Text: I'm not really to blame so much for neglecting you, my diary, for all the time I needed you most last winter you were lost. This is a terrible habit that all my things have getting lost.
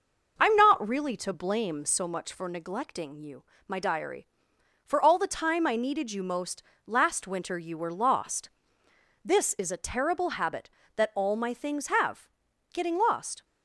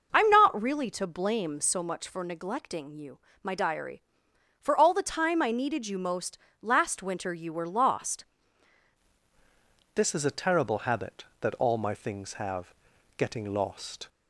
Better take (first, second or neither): first